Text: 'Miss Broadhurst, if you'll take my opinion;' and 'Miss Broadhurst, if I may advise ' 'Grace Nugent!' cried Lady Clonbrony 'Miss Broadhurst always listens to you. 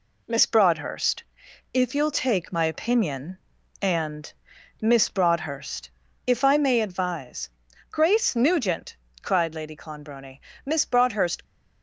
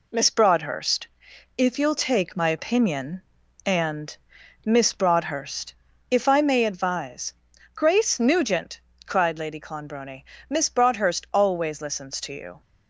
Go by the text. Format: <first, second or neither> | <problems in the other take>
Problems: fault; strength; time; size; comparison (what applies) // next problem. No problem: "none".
second | pauses between "and" and "Miss"; noticeable; at 4.3 s; 0.48 s long; noticeable in the second // pauses between "Clonbrony" and "Miss"; slight; at 10.3 s; 0.26 s long; slight in the second // stops before "always listens to you"; at 11.4 s